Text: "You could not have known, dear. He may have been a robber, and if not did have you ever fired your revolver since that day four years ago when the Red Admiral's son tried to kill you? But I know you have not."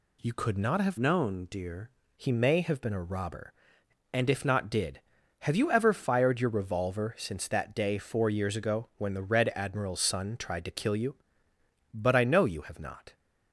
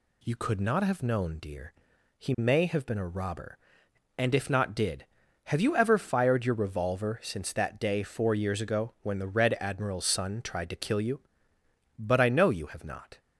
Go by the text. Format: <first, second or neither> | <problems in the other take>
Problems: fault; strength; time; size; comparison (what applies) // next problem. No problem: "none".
second | changes voice from "known" to "dear"; from 0.9 to 1.9 s; 1.0 s long